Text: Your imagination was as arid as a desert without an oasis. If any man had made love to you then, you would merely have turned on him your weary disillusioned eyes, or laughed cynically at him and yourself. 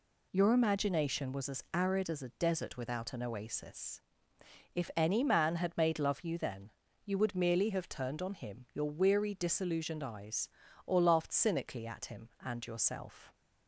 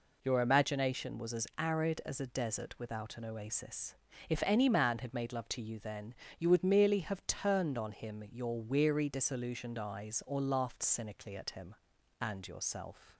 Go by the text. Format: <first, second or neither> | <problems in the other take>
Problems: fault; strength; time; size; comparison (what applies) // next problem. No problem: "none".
second | skips "to"; at 6.2 s